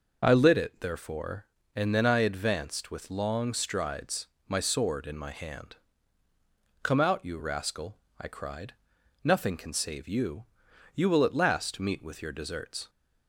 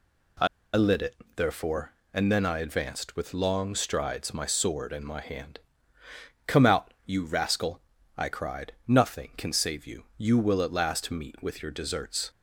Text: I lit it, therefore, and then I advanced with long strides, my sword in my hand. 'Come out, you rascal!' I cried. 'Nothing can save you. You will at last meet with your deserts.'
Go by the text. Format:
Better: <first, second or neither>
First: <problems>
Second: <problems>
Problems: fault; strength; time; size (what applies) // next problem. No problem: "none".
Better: first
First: none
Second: pauses between "I" and "lit"; slight; at 0.4 s; 0.28 s long